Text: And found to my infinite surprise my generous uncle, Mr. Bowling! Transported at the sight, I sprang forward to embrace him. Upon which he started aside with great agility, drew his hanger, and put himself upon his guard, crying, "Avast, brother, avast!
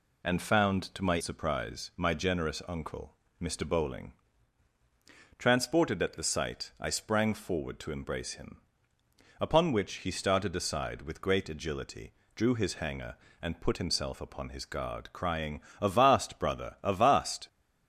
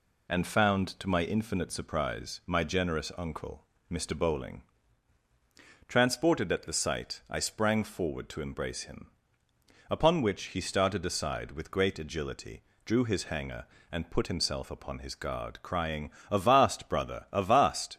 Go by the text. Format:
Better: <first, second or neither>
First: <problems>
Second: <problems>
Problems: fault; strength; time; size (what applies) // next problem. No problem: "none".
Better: second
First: skips "infinite"; at 1.1 s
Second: none